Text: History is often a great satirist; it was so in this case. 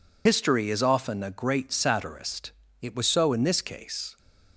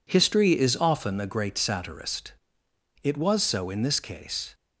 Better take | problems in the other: second | loses the start of "History"; at 0.2 s; 60 ms

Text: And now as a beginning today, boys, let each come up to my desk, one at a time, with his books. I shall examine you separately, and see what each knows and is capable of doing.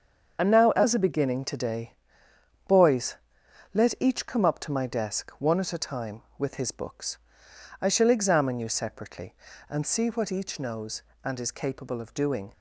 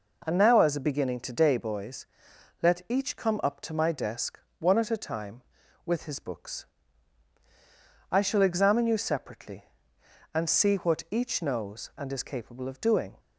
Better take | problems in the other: second | loses the start of "And"; at 0.3 s; 50 ms // starts louder than the rest; until 1.4 s; 7 dB

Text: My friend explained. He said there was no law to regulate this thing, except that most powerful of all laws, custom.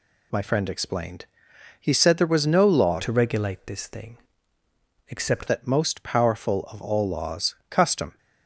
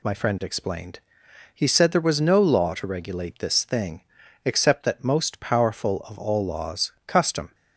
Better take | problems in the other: second | changes voice from "to" to "except"; from 2.9 to 5.4 s; 2.5 s long

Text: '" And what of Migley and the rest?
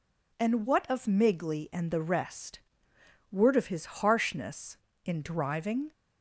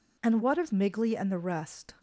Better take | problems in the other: second | goes on to say "Word of his harshness in driving"; strong; from 3.3 s on; 2.5 s long

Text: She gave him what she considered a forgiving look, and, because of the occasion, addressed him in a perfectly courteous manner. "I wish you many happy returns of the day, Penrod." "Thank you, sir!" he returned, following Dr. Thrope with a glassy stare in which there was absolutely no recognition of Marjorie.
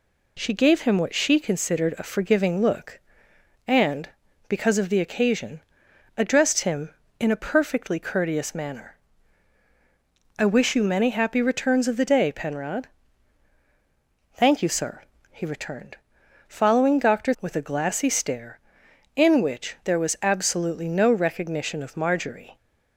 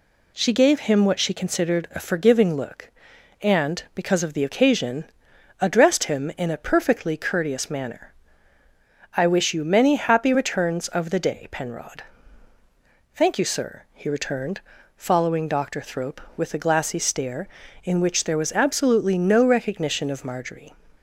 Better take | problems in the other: second | skips "Thrope"; at 17.3 s

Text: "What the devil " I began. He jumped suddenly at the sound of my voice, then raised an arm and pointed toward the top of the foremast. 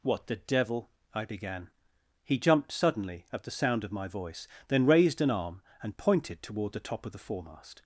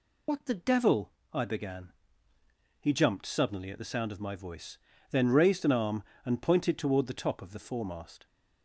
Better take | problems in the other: first | loses the start of "What"; at 0.2 s; 60 ms

